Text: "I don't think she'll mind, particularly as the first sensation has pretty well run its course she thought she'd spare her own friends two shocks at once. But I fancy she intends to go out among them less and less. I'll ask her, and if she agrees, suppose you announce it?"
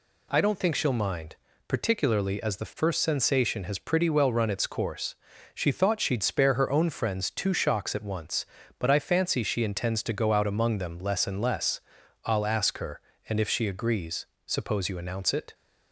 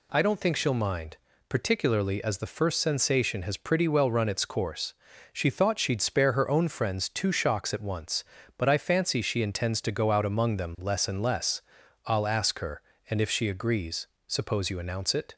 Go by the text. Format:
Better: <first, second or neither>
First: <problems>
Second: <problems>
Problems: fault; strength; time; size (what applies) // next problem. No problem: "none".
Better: neither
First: pauses between "course" and "she"; at 5.1 s; 0.40 s long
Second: pauses between "course" and "she"; at 4.9 s; 0.40 s long